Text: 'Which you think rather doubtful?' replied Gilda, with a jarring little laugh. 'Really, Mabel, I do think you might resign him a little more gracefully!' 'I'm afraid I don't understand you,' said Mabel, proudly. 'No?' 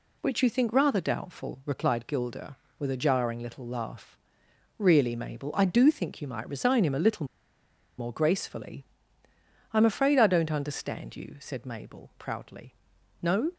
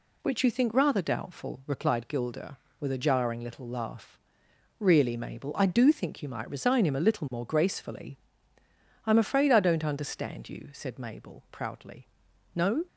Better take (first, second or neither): second